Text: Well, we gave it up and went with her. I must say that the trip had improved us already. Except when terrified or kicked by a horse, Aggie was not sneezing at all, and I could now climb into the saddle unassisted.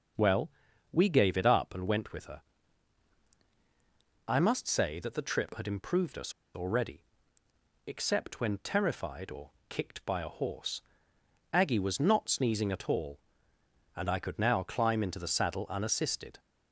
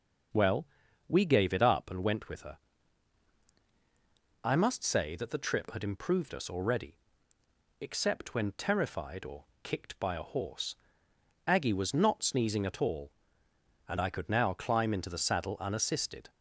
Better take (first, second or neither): second